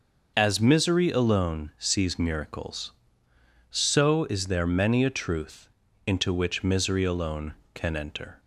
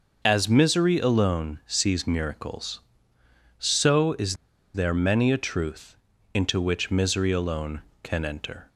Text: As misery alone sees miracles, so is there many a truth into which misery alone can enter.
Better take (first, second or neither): first